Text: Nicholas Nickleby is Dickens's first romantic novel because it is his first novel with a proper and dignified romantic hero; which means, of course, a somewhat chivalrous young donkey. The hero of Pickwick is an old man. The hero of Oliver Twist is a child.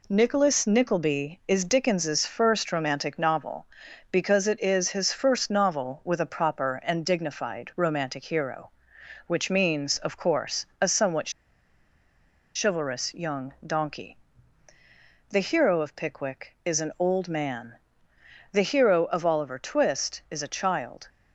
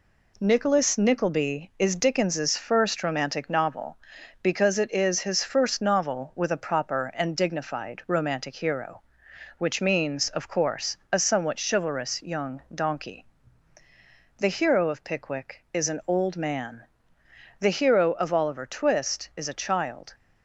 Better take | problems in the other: second | pauses between "somewhat" and "chivalrous"; at 11.3 s; 1.2 s long

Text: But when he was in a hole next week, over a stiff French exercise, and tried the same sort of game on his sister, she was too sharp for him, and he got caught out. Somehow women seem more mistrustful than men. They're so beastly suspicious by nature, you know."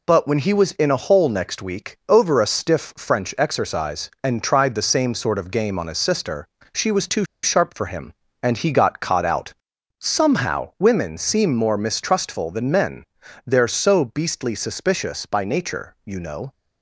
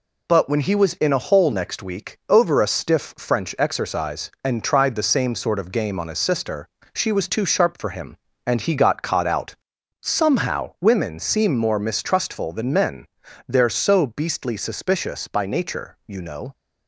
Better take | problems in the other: second | pauses between "too" and "sharp"; slight; at 7.2 s; 0.20 s long

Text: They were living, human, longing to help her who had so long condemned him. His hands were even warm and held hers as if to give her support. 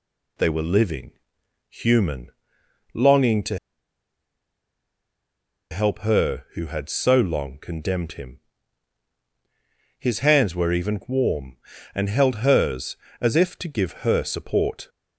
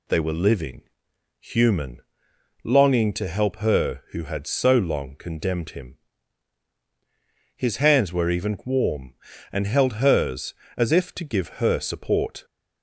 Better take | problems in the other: second | pauses between "to" and "help"; strong; at 3.5 s; 2.1 s long

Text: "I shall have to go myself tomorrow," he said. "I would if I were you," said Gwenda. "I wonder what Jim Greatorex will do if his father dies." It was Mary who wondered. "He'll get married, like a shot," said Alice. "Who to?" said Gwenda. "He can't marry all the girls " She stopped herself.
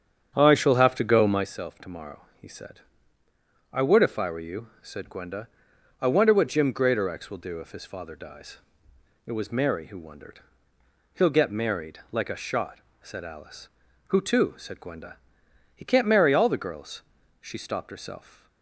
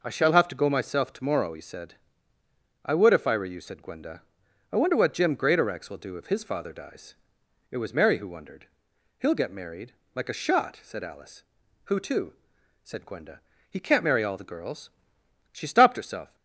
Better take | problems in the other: second | starts louder than the rest; strong; until 1.5 s; 8 dB

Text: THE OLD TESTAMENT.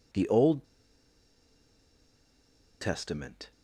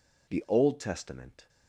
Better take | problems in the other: second | pauses between "OLD" and "TESTAMENT"; strong; at 0.6 s; 2.1 s long

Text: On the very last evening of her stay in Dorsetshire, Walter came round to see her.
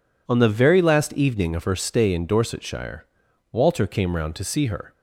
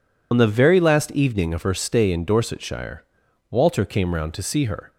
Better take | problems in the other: first | loses the start of "On"; at 0.3 s; 50 ms

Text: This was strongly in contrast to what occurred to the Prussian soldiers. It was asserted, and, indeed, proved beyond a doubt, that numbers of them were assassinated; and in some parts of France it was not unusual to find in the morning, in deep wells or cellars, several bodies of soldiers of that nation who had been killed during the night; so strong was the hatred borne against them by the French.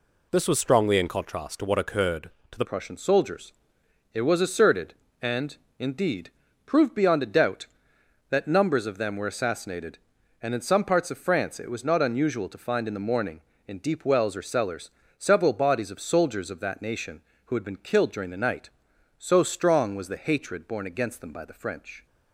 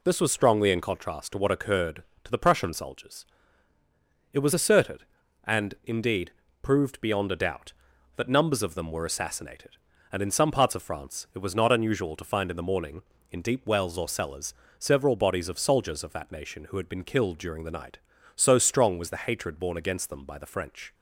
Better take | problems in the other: second | changes voice at "Prussian"; from 2.6 s on; 19.4 s long

